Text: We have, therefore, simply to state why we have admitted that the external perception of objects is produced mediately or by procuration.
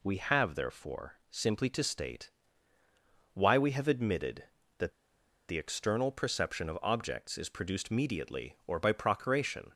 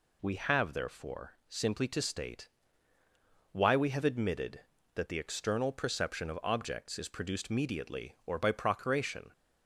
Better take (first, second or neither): second